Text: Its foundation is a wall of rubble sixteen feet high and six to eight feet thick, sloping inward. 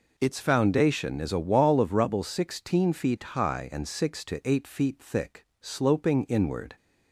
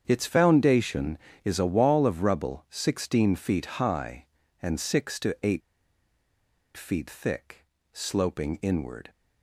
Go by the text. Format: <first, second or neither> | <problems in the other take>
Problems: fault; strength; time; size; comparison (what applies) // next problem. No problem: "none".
first | starts louder than the rest; strong; until 1.0 s; 8 dB // pauses between "eight" and "feet"; at 5.6 s; 1.1 s long